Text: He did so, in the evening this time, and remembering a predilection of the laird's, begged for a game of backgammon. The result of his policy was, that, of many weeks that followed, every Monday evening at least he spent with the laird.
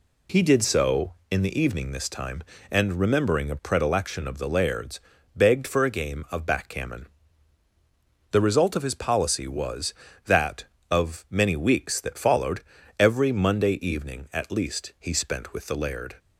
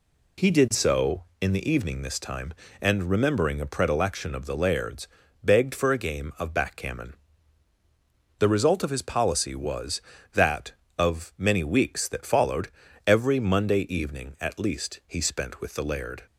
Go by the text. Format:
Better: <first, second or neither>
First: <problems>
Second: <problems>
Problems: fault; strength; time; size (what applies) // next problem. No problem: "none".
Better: neither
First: none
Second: none